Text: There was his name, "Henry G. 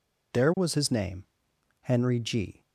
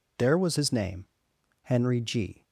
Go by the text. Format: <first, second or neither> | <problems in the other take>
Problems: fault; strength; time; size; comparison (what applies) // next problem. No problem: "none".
neither | none